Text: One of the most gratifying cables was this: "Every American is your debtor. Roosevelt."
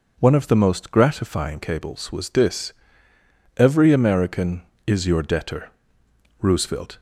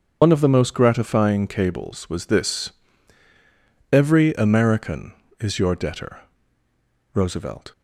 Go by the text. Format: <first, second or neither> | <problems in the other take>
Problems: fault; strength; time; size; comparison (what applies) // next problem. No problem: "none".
first | loses the start of "One"; at 0.2 s; 70 ms // starts louder than the rest; until 1.2 s; 7 dB